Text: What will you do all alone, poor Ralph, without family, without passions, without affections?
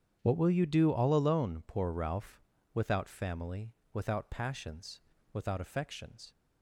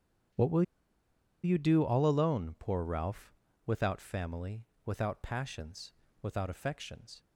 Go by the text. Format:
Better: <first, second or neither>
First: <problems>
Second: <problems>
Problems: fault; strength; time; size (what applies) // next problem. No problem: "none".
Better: first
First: starts louder than the rest; strong; until 1.2 s; 8.5 dB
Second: starts louder than the rest; strong; until 2.1 s; 8.5 dB // pauses between "will" and "you"; noticeable; at 0.6 s; 0.81 s long